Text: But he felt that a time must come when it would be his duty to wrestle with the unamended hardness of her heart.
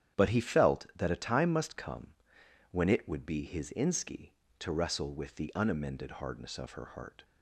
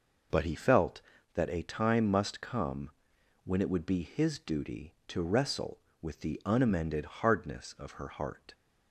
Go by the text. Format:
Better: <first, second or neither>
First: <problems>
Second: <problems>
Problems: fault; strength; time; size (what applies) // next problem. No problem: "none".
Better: second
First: starts louder than the rest; strong; until 1.2 s; 9.5 dB // pauses between "come" and "when"; noticeable; at 2.1 s; 0.56 s long // says "inski" for "duty"; at 3.7 s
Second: pauses between "come" and "when"; noticeable; at 2.8 s; 0.54 s long